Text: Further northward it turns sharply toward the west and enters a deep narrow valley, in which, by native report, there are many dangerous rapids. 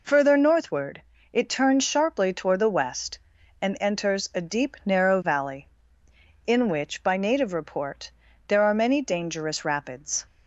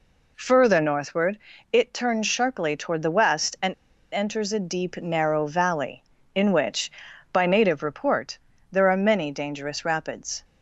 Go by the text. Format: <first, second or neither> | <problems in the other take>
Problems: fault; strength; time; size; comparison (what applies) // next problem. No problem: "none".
first | pauses between "northward" and "it"; slight; at 1.3 s; 0.32 s long; slight in the first // pauses between "and" and "enters"; at 3.7 s; 0.41 s long